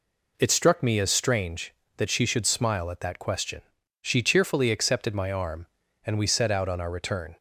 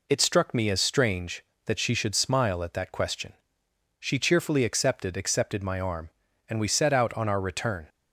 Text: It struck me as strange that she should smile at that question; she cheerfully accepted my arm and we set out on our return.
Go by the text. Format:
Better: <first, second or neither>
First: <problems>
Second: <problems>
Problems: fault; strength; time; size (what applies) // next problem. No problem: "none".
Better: first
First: none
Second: says "accepted" twice; at 5.1 s